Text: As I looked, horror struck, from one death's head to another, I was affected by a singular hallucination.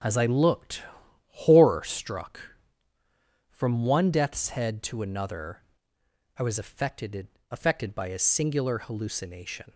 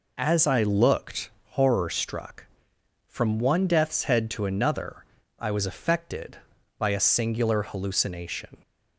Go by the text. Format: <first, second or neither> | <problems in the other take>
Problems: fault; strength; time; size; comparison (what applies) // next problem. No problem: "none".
second | starts louder than the rest; noticeable; until 1.5 s; 6 dB // says "affected" twice; at 7.5 s